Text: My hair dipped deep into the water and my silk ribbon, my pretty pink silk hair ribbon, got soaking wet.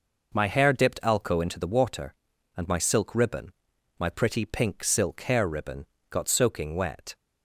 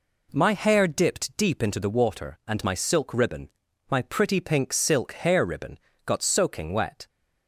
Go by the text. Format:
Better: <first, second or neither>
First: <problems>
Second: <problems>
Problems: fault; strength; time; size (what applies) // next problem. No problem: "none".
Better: second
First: says "alco" for "deep"; at 1.0 s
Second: none